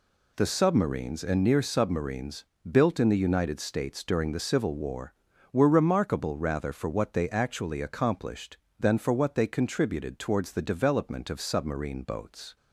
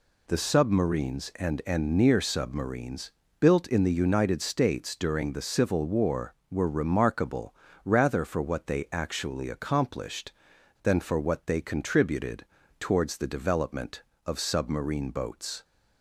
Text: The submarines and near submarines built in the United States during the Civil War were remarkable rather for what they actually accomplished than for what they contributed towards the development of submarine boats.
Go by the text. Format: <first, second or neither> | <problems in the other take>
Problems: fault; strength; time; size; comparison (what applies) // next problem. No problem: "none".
first | says "and" twice; at 1.6 s // pauses between "submarines" and "built"; slight; at 3.1 s; 0.30 s long; slight in the first // pauses between "remarkable" and "rather"; slight; at 7.5 s; 0.30 s long // pauses between "contributed" and "towards"; slight; at 12.4 s; 0.34 s long